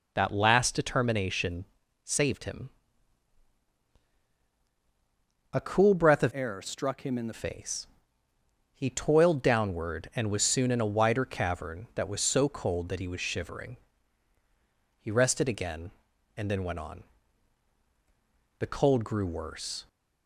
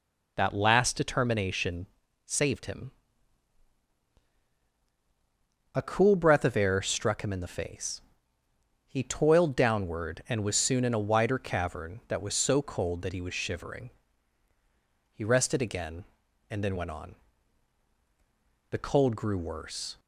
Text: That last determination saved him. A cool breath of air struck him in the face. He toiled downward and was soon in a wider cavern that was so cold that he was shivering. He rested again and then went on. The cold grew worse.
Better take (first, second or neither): second